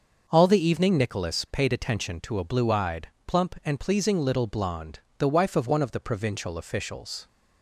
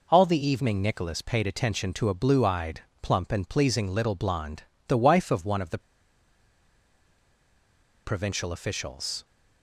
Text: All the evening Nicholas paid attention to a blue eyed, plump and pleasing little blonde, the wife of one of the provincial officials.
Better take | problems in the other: first | pauses between "the" and "provincial"; strong; at 5.7 s; 2.2 s long

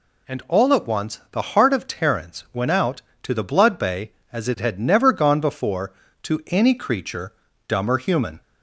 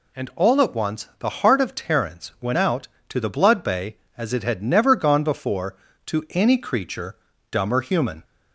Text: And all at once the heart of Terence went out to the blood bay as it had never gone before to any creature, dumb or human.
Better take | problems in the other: neither | none

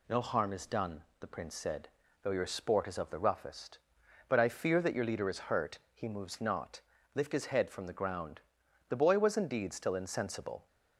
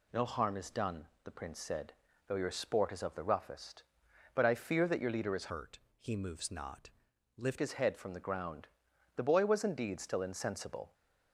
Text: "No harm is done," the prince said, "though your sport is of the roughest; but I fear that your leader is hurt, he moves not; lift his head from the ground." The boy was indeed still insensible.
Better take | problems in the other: first | changes voice from "hurt" to "lift"; from 5.5 to 7.5 s; 2.0 s long

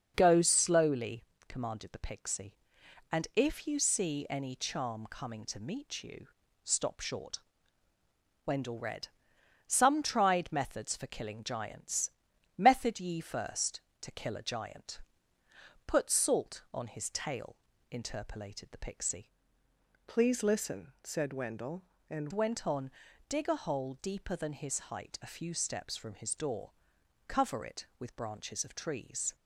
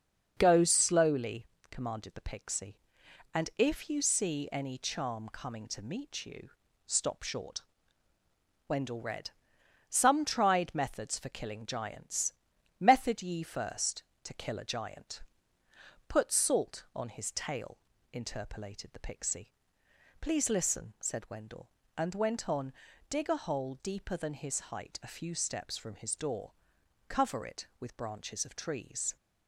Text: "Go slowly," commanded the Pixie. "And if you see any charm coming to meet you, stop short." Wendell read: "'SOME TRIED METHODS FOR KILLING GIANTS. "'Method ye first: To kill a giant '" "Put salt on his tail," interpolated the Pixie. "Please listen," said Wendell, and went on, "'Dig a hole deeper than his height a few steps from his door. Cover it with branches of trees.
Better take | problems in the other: second | starts louder than the rest; until 1.1 s; 6.5 dB; also in the second // changes voice from "Please" to "and"; from 20.0 to 22.2 s; 2.2 s long

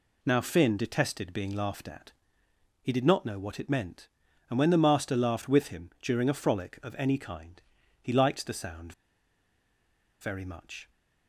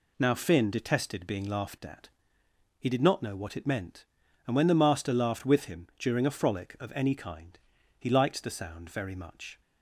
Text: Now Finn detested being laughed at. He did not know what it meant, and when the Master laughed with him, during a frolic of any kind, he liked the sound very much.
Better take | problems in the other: second | pauses between "sound" and "very"; strong; at 8.9 s; 1.2 s long

